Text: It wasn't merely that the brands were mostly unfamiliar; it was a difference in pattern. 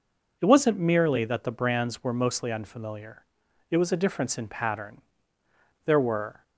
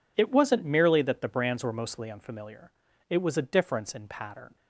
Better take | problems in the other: second | goes on to say "There were"; from 5.8 s on; 0.56 s long

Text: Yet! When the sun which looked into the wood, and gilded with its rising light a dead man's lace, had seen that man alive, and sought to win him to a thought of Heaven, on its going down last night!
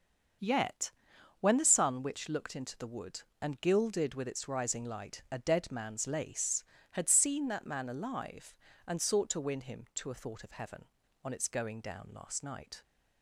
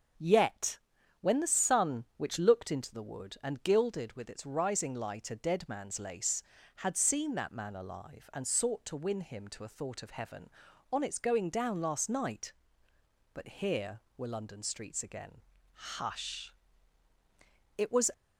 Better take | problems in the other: first | starts louder than the rest; until 1.6 s; 6.5 dB; also in the first // goes on to say "But here were London streets again Hush It was"; strong; from 13.3 s on; 4.7 s long

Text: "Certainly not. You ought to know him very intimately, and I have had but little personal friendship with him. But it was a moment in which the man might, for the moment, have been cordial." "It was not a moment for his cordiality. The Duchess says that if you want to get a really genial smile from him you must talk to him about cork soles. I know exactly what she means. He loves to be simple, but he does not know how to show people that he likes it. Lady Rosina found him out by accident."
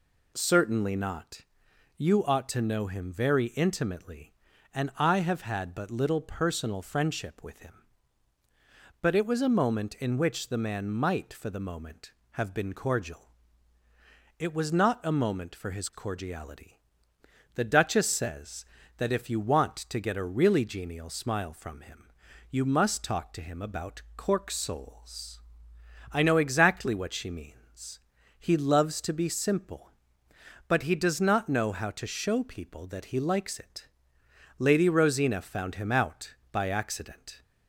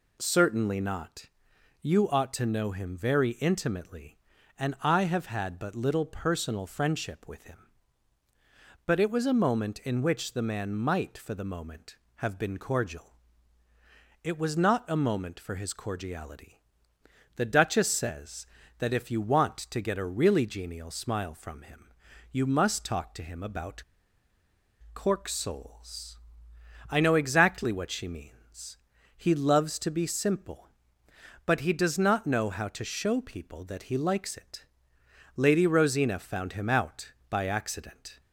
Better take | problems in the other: first | pauses between "him" and "you"; noticeable; at 21.8 s; 0.50 s long; noticeable in the first // pauses between "about" and "cork"; at 23.8 s; 1.1 s long

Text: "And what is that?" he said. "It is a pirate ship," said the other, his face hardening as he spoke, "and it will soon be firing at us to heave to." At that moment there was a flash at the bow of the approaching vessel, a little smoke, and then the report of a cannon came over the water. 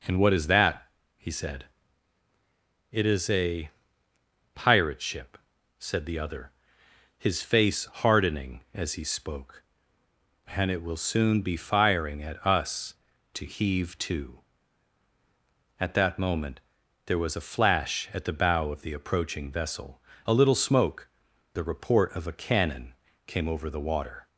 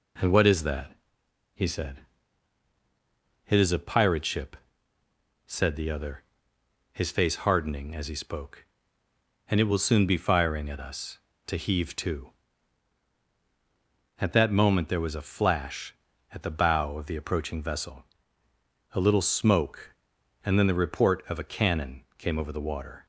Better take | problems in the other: second | pauses between "a" and "pirate"; noticeable; at 3.7 s; 0.84 s long // pauses between "moment" and "there"; noticeable; at 16.5 s; 0.46 s long // skips "and then"; at 21.3 s // pauses between "cannon" and "came"; slight; at 22.9 s; 0.32 s long

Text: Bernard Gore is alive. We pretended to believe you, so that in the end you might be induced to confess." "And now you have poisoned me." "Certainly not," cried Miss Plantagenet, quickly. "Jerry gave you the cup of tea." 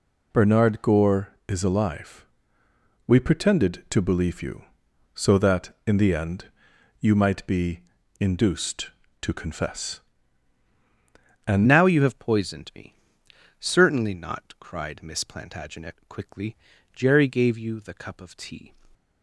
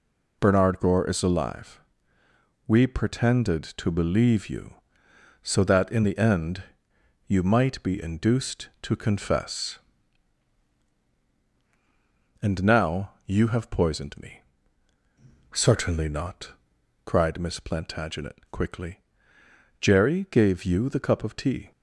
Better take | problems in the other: second | pauses between "end" and "you"; noticeable; at 6.4 s; 0.54 s long; noticeable in the second // pauses between "be" and "induced"; at 7.8 s; 0.40 s long // changes voice at "now"; from 11.6 s on; 7.1 s long

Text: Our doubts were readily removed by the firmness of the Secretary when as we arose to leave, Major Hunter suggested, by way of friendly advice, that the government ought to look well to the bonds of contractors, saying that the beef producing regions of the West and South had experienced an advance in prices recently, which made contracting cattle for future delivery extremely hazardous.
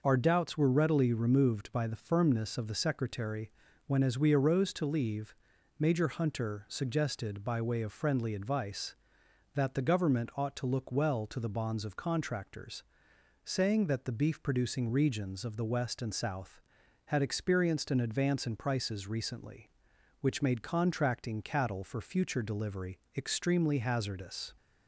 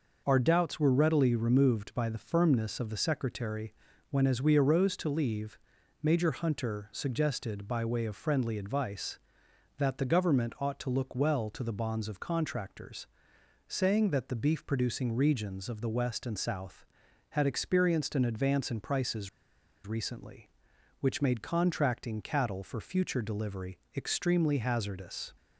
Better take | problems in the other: first | pauses between "Secretary" and "when"; at 3.7 s; 0.38 s long; also in the first // pauses between "prices" and "recently"; noticeable; at 19.2 s; 0.57 s long // pauses between "delivery" and "extremely"; slight; at 23.7 s; 0.16 s long; slight in the first

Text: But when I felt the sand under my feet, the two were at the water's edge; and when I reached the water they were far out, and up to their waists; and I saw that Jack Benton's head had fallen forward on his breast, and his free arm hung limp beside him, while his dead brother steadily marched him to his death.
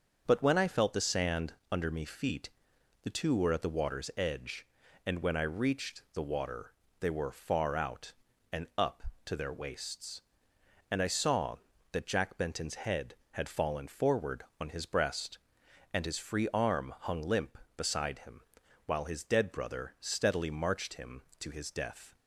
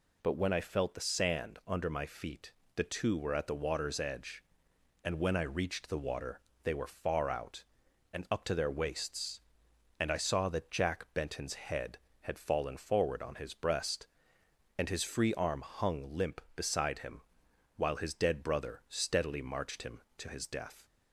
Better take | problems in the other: second | starts louder than the rest; noticeable; until 1.2 s; 6 dB // pauses between "sand" and "under"; slight; at 1.5 s; 0.18 s long // says "me" for "my"; at 1.9 s // pauses between "water" and "they"; slight; at 6.7 s; 0.26 s long; slight in the second

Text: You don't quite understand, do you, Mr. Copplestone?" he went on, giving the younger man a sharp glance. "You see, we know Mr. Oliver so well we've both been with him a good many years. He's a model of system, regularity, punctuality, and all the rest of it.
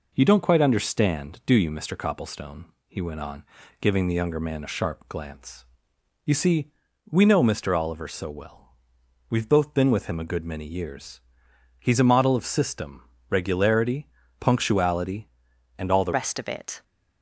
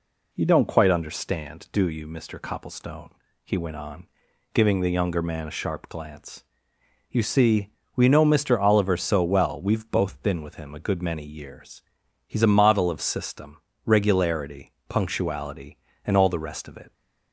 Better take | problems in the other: second | pauses between "well" and "we've"; noticeable; at 8.7 s; 0.56 s long // changes voice at "rest"; from 16.1 s on; 0.7 s long

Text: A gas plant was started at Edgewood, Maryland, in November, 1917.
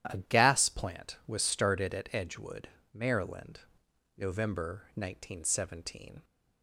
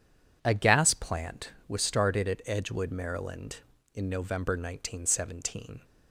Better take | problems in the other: second | starts louder than the rest; strong; until 1.0 s; 11 dB // skips "in"; at 3.8 s

